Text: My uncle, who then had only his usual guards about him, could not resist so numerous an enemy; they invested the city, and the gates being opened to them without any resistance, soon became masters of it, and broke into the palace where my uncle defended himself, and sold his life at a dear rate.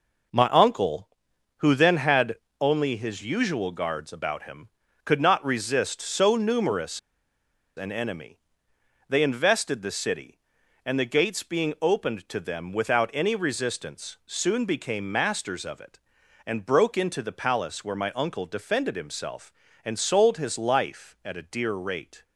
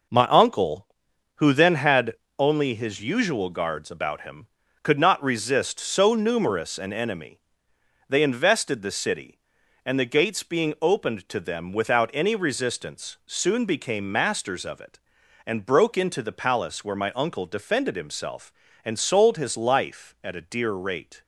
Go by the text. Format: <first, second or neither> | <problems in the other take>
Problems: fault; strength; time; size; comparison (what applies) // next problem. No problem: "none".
second | pauses between "had" and "only"; slight; at 2.3 s; 0.24 s long; slight in the second // pauses between "numerous" and "an"; noticeable; at 6.9 s; 0.77 s long